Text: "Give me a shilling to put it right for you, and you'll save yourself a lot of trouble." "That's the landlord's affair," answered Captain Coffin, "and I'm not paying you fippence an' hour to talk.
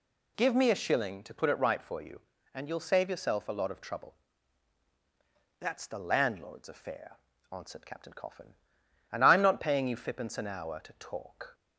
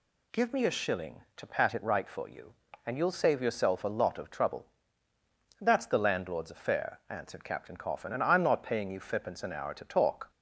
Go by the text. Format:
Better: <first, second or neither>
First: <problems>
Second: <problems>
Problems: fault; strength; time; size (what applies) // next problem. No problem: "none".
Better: first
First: none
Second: says "pat" for "put"; at 1.4 s